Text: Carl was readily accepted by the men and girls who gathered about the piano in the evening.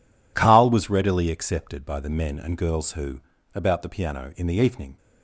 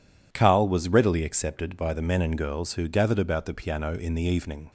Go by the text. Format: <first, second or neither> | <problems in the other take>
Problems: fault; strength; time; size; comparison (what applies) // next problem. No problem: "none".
second | skips "gathered"; at 3.3 s